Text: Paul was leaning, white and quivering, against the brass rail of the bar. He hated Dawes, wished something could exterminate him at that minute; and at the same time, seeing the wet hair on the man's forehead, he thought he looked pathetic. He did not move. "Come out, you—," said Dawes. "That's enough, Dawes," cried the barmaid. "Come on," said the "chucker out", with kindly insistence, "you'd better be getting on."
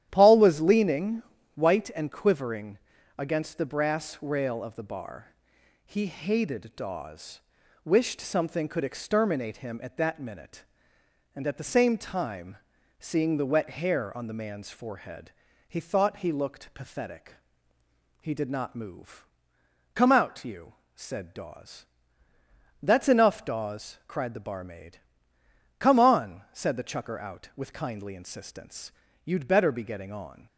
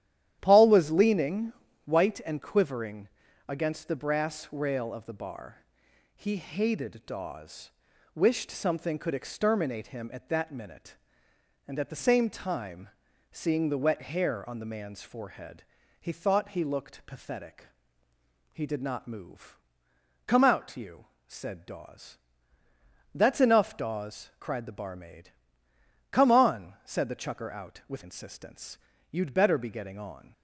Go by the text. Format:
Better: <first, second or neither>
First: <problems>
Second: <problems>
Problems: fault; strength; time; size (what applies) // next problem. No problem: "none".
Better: first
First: starts louder than the rest; strong; until 1.1 s; 11.5 dB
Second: starts louder than the rest; strong; until 1.4 s; 11 dB // skips "kindly"; at 28.0 s